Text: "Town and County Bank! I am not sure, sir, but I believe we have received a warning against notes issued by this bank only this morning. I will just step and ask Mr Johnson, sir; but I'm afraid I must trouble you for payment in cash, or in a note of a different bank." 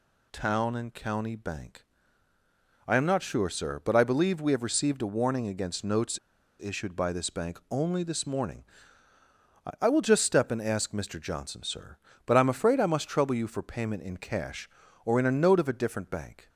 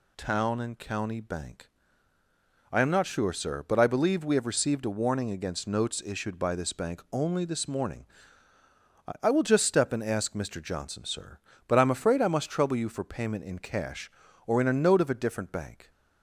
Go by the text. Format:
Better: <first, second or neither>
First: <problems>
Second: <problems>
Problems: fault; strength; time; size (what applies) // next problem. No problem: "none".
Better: second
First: pauses between "notes" and "issued"; at 6.1 s; 0.44 s long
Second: none